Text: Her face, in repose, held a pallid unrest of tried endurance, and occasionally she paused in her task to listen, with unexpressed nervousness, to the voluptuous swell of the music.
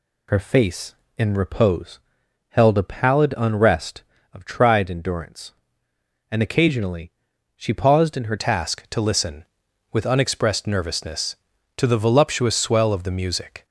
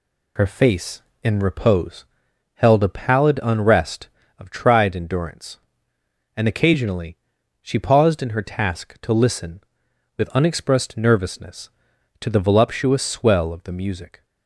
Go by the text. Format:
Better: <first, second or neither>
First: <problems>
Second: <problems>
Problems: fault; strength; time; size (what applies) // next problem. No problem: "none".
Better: second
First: pauses between "occasionally" and "she"; noticeable; at 7.0 s; 0.46 s long // changes voice at "task"; from 8.3 s on; 5.3 s long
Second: pauses between "occasionally" and "she"; noticeable; at 7.1 s; 0.46 s long